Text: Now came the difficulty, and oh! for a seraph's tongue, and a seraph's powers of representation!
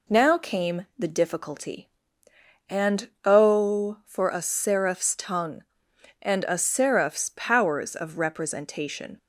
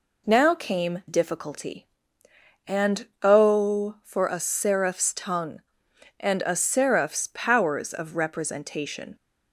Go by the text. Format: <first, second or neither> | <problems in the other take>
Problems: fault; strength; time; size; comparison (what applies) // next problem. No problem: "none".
first | skips "the"; at 1.0 s